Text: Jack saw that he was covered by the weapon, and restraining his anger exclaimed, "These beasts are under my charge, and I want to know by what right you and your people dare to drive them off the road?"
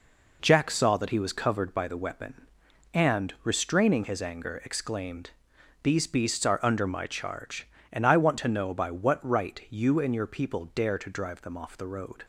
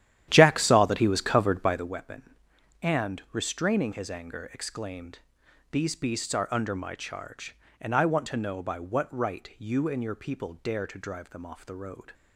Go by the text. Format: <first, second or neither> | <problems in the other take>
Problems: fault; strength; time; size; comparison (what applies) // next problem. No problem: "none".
first | starts louder than the rest; strong; until 1.9 s; 11.5 dB